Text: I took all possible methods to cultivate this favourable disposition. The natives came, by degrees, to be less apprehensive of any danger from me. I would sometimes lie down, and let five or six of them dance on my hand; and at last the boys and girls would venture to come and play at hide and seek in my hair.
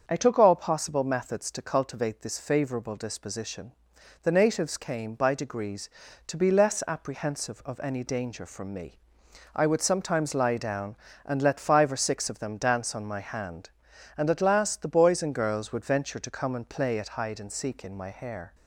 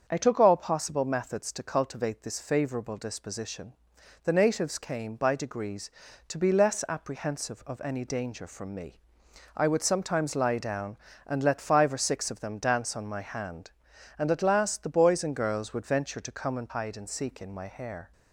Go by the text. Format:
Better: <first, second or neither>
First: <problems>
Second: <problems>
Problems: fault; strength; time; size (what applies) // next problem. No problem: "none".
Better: first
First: starts louder than the rest; until 1.0 s; 7 dB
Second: starts louder than the rest; strong; until 1.0 s; 7 dB // skips "play at"; at 16.7 s